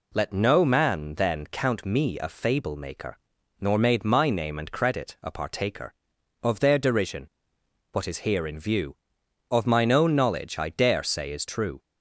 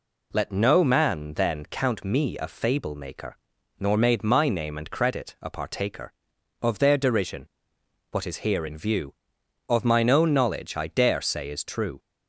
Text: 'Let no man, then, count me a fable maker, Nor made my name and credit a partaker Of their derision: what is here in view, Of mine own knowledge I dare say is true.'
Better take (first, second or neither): neither